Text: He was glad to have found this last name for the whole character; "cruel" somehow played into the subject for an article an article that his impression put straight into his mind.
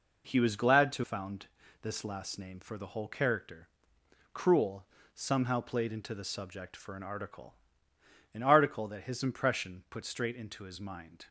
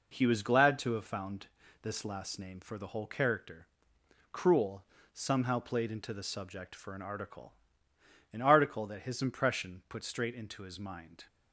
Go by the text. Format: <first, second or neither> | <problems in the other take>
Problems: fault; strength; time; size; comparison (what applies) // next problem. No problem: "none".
second | skips "have"; at 1.0 s // pauses between "found" and "this"; slight; at 1.4 s; 0.34 s long; slight in the second // pauses between "cruel" and "somehow"; slight; at 4.8 s; 0.28 s long; slight in the second // pauses between "article" and "an"; noticeable; at 7.5 s; 0.80 s long; noticeable in the second